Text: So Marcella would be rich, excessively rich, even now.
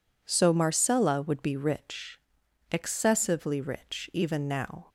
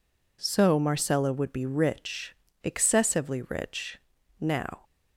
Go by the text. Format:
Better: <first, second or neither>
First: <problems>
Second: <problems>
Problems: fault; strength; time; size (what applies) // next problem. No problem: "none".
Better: first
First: none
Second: skips "even"; at 4.1 s